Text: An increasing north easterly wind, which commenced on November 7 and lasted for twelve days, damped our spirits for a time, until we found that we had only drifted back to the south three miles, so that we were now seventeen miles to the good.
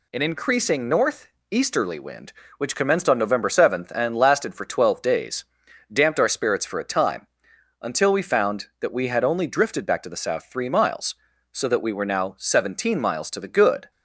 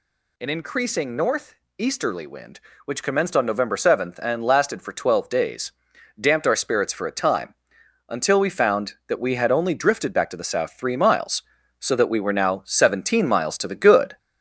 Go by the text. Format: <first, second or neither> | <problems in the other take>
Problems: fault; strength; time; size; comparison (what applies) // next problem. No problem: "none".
first | gets louder; noticeable; throughout; 5 dB // pauses between "north" and "easterly"; slight; at 1.5 s; 0.22 s long; slight in the first